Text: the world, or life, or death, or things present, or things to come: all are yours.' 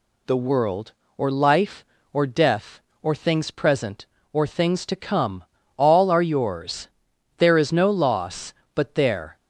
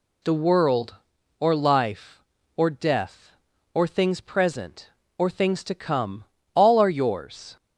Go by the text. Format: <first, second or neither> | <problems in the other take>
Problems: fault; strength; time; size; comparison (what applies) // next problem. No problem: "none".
second | goes on to say "There is no loss but there"; strong; from 7.3 s on; 1.9 s long